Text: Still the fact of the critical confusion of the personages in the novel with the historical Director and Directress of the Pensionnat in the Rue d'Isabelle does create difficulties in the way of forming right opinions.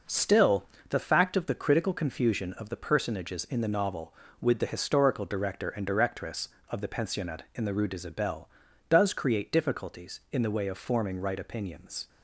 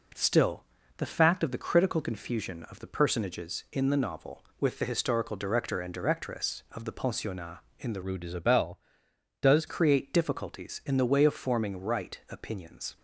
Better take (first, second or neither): first